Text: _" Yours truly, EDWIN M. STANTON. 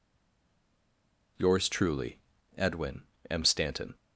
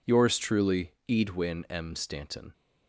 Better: second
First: stays silent before the first word; noticeable; until 1.3 s; 1.3 s long // pauses between "EDWIN" and "M"; slight; at 3.0 s; 0.26 s long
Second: none

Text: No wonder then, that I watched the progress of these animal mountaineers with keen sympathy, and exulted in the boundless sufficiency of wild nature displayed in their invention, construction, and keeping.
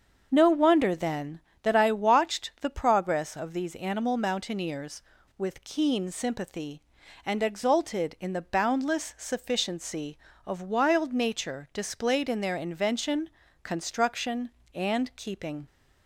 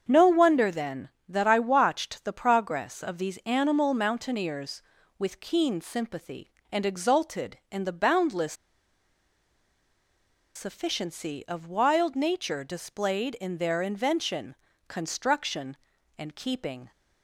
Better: first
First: starts louder than the rest; until 1.3 s; 7 dB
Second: starts louder than the rest; strong; until 1.1 s; 7 dB // pauses between "boundless" and "sufficiency"; strong; at 8.5 s; 2.0 s long

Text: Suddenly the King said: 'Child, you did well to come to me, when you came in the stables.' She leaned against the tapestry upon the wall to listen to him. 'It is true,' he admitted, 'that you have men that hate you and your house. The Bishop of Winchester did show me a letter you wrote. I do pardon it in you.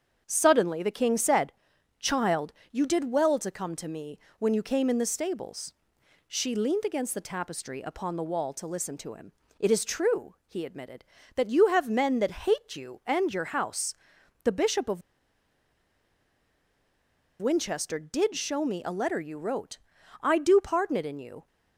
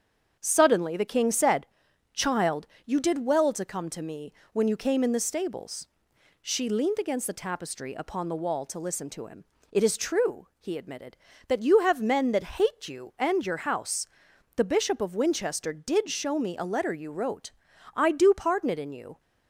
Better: second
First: starts louder than the rest; strong; until 1.2 s; 7.5 dB // pauses between "of" and "Winchester"; strong; at 15.0 s; 2.4 s long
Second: starts louder than the rest; strong; until 1.4 s; 7.5 dB

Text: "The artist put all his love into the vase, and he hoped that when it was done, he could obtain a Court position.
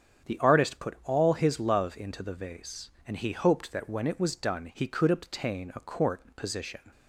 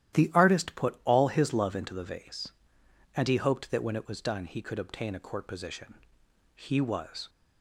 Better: first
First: starts louder than the rest; strong; until 1.3 s; 8 dB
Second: starts louder than the rest; strong; until 1.1 s; 12 dB // goes on to say "He was"; noticeable; from 6.5 s on; 0.76 s long

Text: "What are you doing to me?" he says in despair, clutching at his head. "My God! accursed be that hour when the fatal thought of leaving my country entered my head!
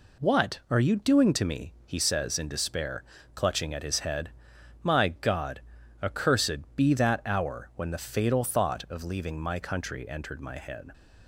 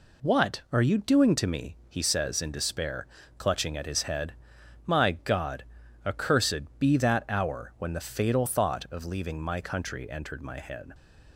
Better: neither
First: none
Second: none

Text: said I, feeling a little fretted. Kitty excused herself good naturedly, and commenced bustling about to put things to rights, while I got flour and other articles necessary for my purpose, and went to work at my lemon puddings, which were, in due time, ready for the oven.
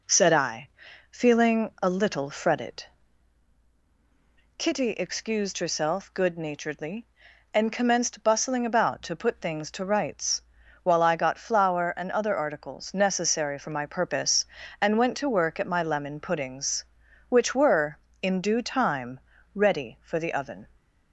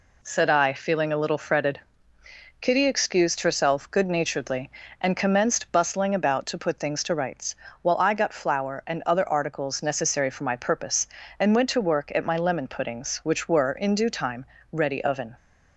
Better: first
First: none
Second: skips "for the"; at 15.0 s

